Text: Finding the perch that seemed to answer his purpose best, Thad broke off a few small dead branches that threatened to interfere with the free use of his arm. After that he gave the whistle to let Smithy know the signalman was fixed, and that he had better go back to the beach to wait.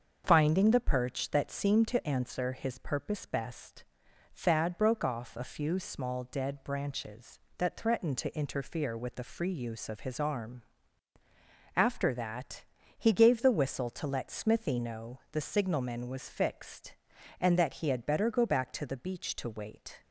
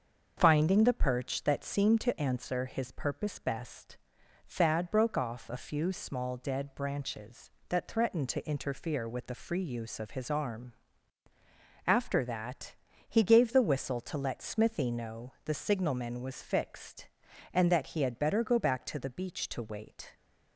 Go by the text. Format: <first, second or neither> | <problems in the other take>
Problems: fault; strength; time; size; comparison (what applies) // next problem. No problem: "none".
neither | starts louder than the rest; the same in both // pauses between "that" and "he"; slight; the same in both